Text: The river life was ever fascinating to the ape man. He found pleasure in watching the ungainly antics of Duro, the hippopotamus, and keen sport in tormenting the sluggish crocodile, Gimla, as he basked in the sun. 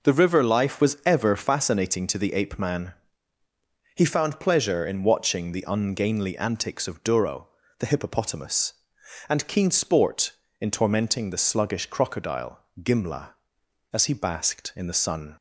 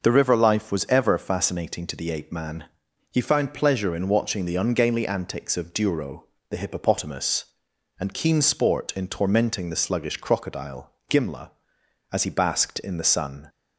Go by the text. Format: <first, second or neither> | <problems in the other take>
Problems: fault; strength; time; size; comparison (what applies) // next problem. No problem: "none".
neither | none